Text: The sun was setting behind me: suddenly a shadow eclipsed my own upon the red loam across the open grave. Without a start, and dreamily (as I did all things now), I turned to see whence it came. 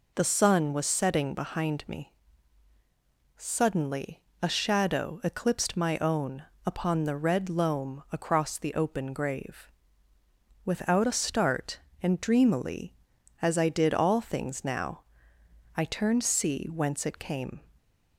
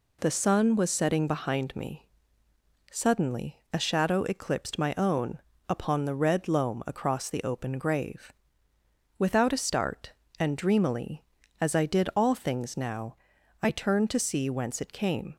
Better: second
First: pauses between "suddenly" and "a"; slight; at 4.1 s; 0.24 s long // pauses between "own" and "upon"; slight; at 6.4 s; 0.22 s long // skips "to"; at 16.2 s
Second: pauses between "own" and "upon"; slight; at 5.3 s; 0.30 s long

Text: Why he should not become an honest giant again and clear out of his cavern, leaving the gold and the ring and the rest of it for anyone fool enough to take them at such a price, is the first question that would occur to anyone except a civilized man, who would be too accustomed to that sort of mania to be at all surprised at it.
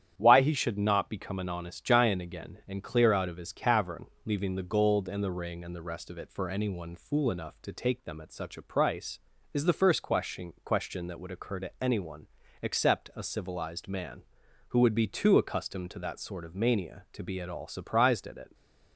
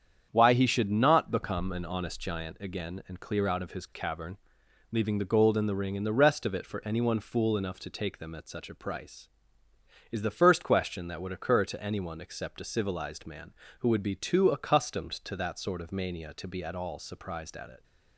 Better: second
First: starts louder than the rest; strong; until 1.1 s; 10 dB // says "question" twice; at 10.6 s // pauses between "anyone" and "except"; slight; at 12.2 s; 0.34 s long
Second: starts louder than the rest; strong; until 1.3 s; 8 dB

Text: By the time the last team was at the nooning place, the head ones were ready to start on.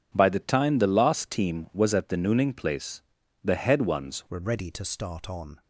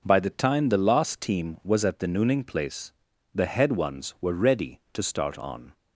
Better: second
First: changes voice at "were"; from 4.2 s on; 1.4 s long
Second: none

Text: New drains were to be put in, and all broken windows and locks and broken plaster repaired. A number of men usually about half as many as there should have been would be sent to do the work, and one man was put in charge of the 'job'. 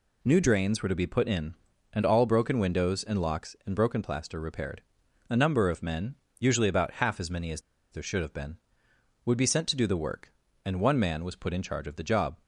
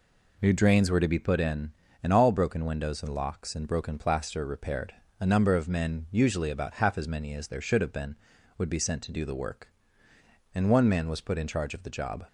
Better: second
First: pauses between "men" and "usually"; slight; at 6.1 s; 0.24 s long // pauses between "as" and "there"; slight; at 7.6 s; 0.30 s long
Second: none

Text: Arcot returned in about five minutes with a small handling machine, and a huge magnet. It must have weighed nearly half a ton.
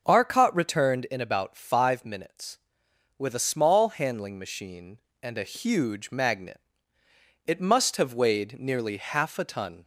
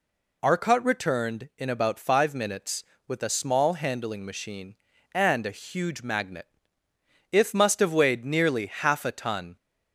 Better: first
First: none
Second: says "If" for "It"; at 7.3 s

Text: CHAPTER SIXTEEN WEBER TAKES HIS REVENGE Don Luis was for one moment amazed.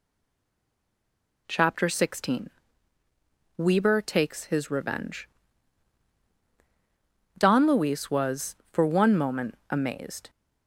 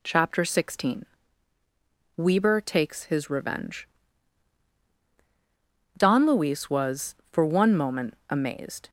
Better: second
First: stays silent before the first word; noticeable; until 1.4 s; 1.4 s long // pauses between "SIXTEEN" and "WEBER"; at 2.4 s; 1.0 s long // pauses between "REVENGE" and "Don"; strong; at 5.2 s; 2.1 s long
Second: pauses between "SIXTEEN" and "WEBER"; at 1.0 s; 1.1 s long // pauses between "REVENGE" and "Don"; strong; at 3.8 s; 2.1 s long

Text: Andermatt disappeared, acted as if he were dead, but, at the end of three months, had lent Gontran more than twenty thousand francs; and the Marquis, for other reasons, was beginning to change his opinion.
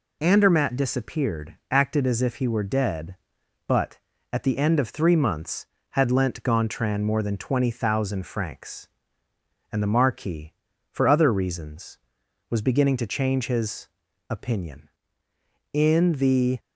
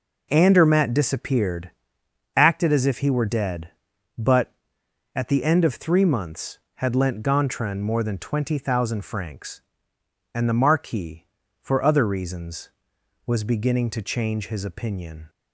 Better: second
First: pauses between "his" and "opinion"; at 13.8 s; 0.42 s long // goes on to say "In the"; noticeable; from 15.7 s on; 0.88 s long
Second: none

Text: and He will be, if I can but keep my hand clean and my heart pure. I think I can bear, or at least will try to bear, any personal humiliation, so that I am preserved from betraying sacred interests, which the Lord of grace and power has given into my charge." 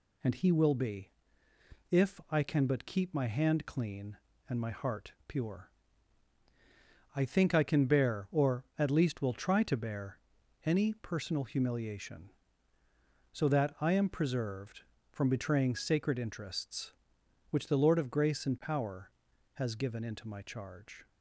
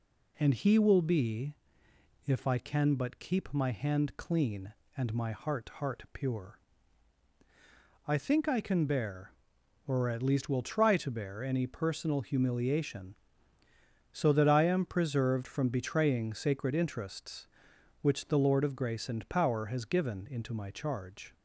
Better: first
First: none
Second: says "heart" twice; at 5.7 s

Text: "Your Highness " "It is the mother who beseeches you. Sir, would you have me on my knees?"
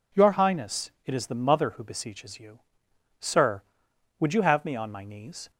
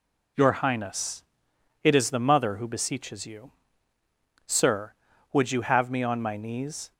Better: neither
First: none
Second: none

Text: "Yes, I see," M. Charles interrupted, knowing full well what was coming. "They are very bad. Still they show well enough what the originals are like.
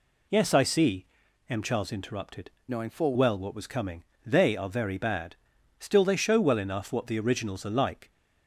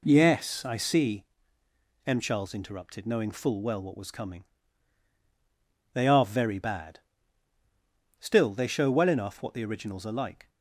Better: second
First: changes voice from "knowing" to "full"; from 2.6 to 3.1 s; 0.5 s long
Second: none

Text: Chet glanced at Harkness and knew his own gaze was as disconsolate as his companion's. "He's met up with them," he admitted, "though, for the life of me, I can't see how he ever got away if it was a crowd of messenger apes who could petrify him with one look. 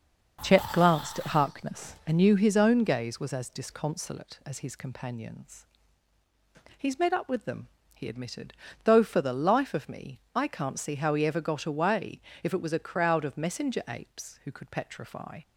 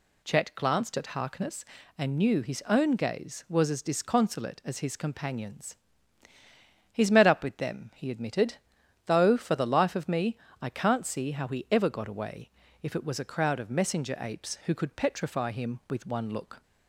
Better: second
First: starts louder than the rest; until 1.5 s; 6.5 dB // pauses between "away" and "if"; slight; at 12.1 s; 0.22 s long // stops before "him with one look"; at 15.4 s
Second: pauses between "away" and "if"; slight; at 12.5 s; 0.32 s long

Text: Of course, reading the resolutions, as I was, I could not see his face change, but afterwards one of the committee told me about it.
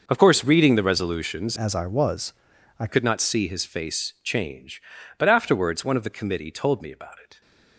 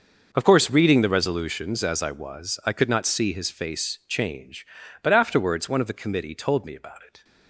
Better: second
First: changes voice from "as" to "I"; from 1.5 to 2.8 s; 1.3 s long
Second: none

